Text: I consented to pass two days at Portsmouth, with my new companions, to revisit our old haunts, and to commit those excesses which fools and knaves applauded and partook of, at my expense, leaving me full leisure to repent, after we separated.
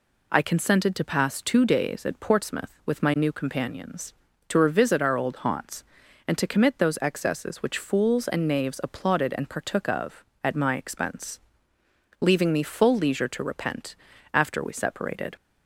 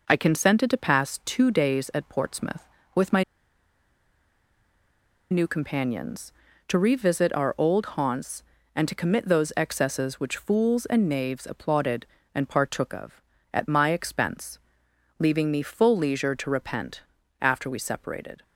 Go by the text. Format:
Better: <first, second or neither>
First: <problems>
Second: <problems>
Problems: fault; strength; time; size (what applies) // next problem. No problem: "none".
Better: first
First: none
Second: pauses between "my" and "new"; strong; at 3.2 s; 2.0 s long